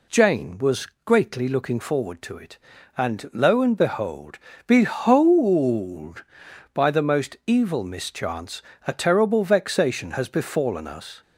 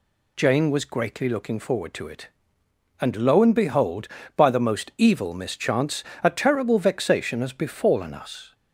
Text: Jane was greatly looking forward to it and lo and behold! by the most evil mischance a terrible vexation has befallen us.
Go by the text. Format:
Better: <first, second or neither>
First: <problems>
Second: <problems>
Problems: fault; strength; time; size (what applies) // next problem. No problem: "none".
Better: second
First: pauses between "was" and "greatly"; slight; at 0.8 s; 0.18 s long // says "behold" twice; at 4.6 s // pauses between "mischance" and "a"; slight; at 8.6 s; 0.24 s long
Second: pauses between "mischance" and "a"; slight; at 6.0 s; 0.20 s long